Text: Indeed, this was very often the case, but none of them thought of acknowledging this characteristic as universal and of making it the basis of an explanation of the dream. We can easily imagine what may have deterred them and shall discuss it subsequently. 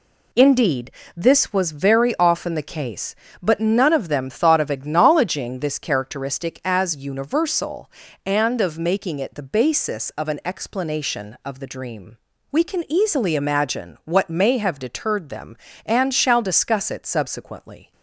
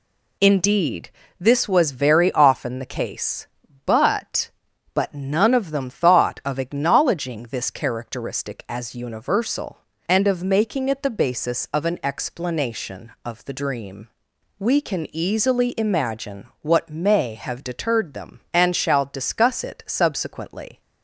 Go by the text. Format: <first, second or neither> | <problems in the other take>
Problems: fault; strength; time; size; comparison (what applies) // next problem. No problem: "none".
first | says "but" twice; at 4.9 s // pauses between "imagine" and "what"; slight; at 16.4 s; 0.16 s long